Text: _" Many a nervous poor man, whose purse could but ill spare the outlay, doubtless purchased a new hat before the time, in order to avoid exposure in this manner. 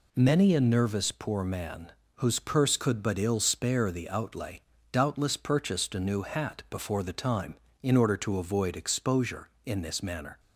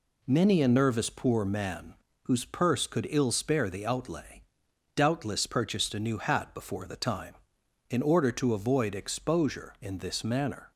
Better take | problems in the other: first | skips "but"; at 3.0 s

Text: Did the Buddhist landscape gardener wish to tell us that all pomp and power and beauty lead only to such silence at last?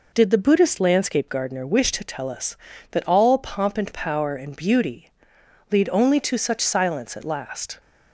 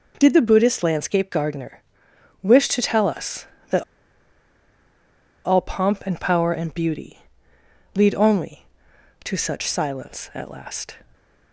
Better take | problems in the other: first | pauses between "gardener" and "wish"; noticeable; at 1.8 s; 0.60 s long // pauses between "that" and "all"; strong; at 3.8 s; 1.6 s long // pauses between "beauty" and "lead"; noticeable; at 7.2 s; 0.74 s long; noticeable in the first

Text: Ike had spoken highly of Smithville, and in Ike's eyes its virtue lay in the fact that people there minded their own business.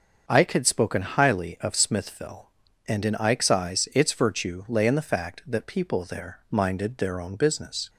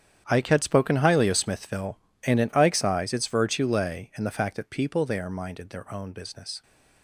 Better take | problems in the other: first | gets quieter; strong; throughout; 15 dB // starts louder than the rest; strong; until 1.3 s; 9 dB; also in the first

